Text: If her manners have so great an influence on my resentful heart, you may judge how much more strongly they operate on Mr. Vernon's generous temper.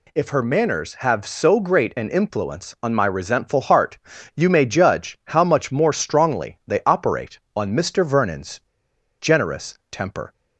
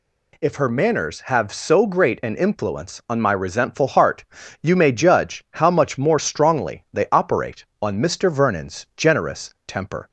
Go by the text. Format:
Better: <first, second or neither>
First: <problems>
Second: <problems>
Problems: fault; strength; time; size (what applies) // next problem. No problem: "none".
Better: second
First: pauses between "Vernon's" and "generous"; noticeable; at 8.6 s; 0.58 s long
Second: none